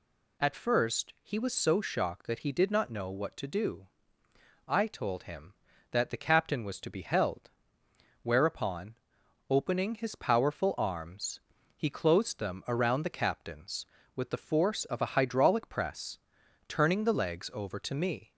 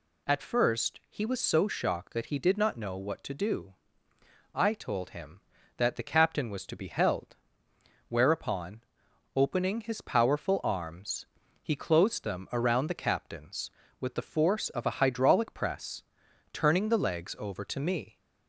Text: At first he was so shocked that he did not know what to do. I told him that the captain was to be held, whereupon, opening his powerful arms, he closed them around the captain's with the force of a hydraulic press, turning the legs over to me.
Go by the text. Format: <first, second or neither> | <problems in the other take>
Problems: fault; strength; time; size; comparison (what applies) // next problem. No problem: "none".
neither | none